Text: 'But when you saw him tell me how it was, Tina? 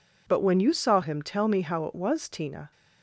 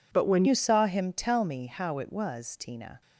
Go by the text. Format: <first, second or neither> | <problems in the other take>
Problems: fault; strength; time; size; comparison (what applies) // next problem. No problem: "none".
first | changes voice at "you"; from 0.4 s on; 2.6 s long